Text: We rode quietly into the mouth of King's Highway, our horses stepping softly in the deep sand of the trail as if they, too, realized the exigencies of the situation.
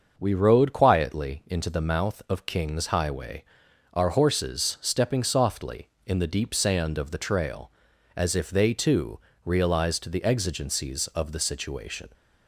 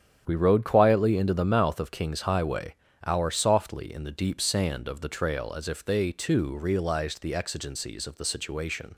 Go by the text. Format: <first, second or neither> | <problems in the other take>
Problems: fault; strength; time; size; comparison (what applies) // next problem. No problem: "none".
first | starts louder than the rest; strong; until 1.2 s; 9 dB; also in the first // skips "horses stepping"; at 3.2 s